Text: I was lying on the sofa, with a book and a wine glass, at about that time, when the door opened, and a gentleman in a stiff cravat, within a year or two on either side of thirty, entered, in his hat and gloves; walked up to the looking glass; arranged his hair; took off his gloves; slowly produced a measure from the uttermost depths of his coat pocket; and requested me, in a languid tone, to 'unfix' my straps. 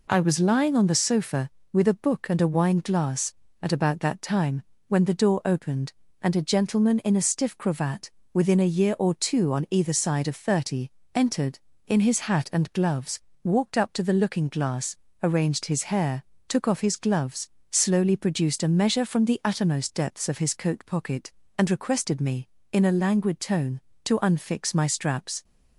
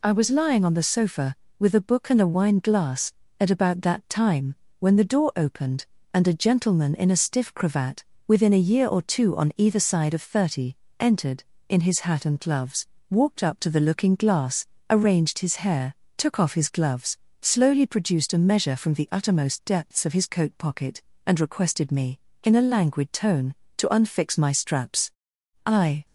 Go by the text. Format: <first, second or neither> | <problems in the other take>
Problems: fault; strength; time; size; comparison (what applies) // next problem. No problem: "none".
first | goes on to say "I"; slight; from 25.6 s on; 0.40 s long